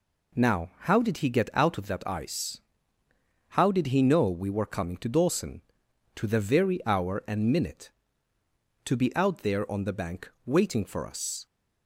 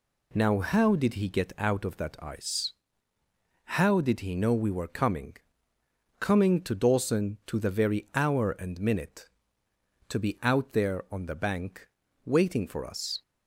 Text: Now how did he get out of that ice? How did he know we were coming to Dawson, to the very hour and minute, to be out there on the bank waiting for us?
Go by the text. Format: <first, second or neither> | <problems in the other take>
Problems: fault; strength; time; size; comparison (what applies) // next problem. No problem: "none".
first | says "coming" twice; at 6.1 s // pauses between "bank" and "waiting"; slight; at 11.8 s; 0.36 s long; slight in the first